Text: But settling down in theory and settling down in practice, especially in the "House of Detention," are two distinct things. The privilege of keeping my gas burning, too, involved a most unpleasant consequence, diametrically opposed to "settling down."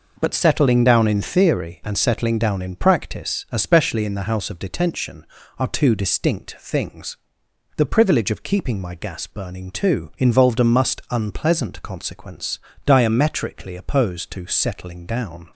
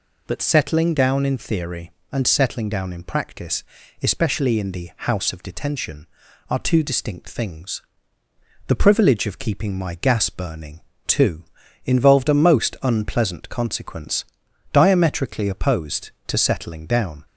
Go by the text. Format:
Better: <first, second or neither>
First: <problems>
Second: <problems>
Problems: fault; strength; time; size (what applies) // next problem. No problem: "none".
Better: second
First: says "must" for "most"; at 10.6 s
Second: none